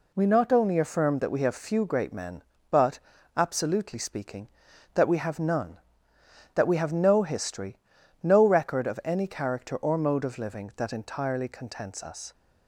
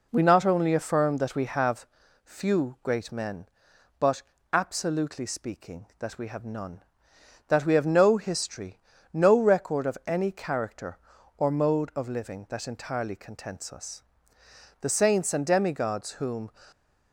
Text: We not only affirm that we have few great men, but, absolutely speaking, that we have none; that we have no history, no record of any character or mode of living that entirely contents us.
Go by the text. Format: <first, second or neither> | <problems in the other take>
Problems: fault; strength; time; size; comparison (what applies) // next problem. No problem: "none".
first | pauses between "have" and "few"; at 1.8 s; 0.38 s long // goes on to say "The saints and demigods whom"; strong; from 14.8 s on; 1.7 s long